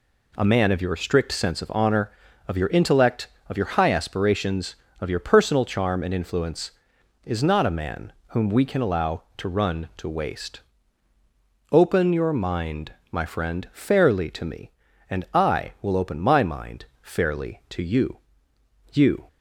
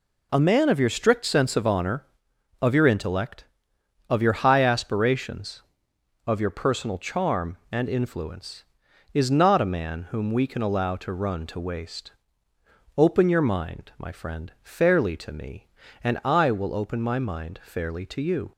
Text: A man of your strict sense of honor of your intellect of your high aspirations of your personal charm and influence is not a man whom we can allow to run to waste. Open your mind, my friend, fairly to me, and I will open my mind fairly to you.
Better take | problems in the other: second | pauses between "mind" and "fairly"; slight; at 16.8 s; 0.16 s long // says "you" twice; at 18.9 s

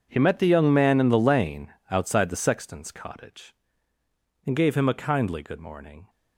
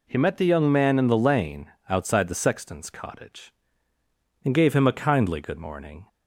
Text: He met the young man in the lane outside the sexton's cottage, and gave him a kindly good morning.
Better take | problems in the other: second | gets quieter; strong; throughout; 16.5 dB // pauses between "lane" and "outside"; slight; at 1.7 s; 0.20 s long; slight in the second

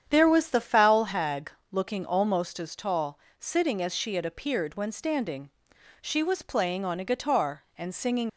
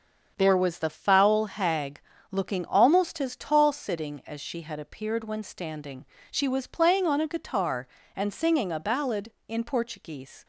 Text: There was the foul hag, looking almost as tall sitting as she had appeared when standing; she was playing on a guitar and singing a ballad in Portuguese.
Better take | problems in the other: second | starts louder than the rest; strong; until 1.1 s; 8.5 dB; also in the second // pauses between "tall" and "sitting"; slight; at 3.1 s; 0.20 s long // stops before "a ballad in Portuguese"; at 8.2 s

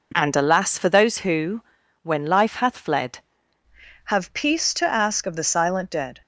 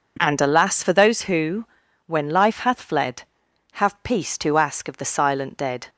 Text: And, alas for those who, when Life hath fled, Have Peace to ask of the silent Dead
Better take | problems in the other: second | changes voice at "Have"; from 4.0 s on; 2.2 s long

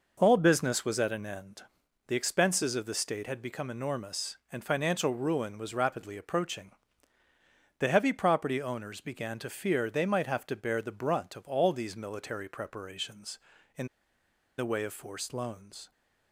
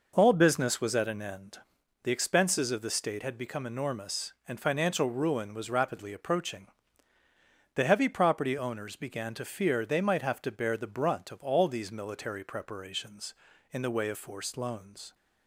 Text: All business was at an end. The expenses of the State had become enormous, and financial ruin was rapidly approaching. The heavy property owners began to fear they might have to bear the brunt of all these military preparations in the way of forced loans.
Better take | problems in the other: second | pauses between "in" and "the"; noticeable; at 13.8 s; 0.71 s long

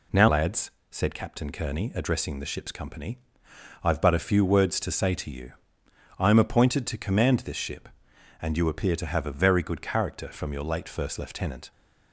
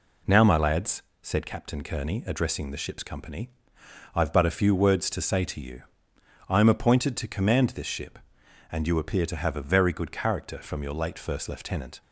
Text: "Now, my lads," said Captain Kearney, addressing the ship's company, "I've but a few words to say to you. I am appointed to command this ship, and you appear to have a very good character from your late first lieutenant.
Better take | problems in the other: second | skips "my"; at 0.2 s

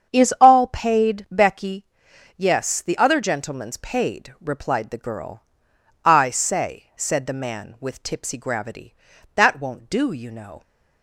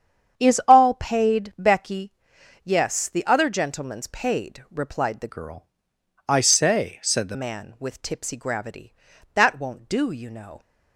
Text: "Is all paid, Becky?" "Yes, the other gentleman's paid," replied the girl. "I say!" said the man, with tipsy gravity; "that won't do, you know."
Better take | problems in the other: first | starts louder than the rest; strong; until 1.4 s; 8 dB; strong in the first // changes voice from "girl" to "the"; from 5.2 to 7.3 s; 2.1 s long

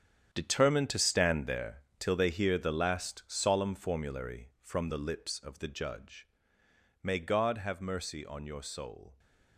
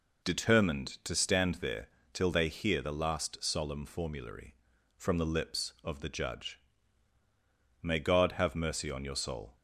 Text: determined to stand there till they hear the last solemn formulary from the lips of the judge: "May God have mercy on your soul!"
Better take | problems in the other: second | gets quieter; strong; throughout; 11.5 dB // pauses between "there" and "till"; slight; at 1.7 s; 0.20 s long; slight in the second

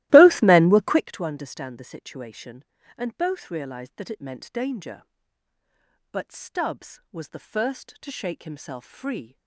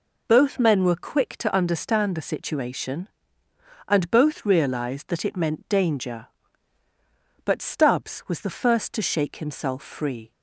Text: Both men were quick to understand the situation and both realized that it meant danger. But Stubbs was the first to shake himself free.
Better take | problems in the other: second | starts louder than the rest; strong; until 1.1 s; 16.5 dB

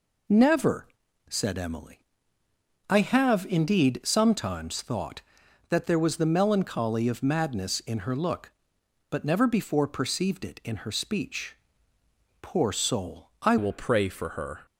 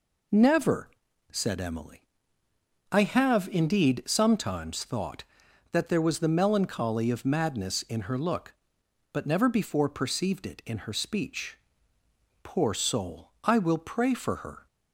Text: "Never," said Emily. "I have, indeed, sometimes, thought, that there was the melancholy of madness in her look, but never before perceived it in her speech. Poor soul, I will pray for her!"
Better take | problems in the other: second | changes voice at "will"; from 13.5 s on; 1.1 s long

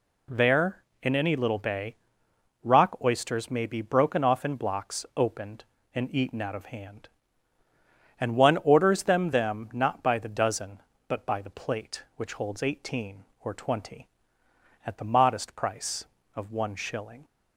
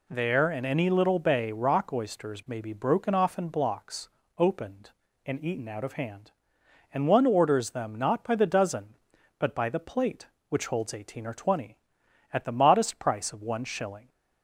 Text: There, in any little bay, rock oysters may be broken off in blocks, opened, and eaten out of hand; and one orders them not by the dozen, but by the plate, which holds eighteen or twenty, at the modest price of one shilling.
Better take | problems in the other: second | says "them" twice; at 9.3 s

